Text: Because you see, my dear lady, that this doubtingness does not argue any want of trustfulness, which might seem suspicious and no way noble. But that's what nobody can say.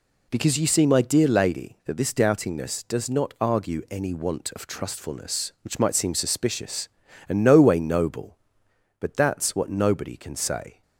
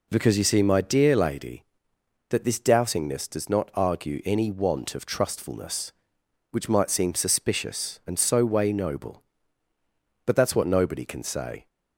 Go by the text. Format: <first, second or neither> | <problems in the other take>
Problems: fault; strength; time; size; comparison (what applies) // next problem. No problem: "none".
first | says "so" for "no"; at 8.1 s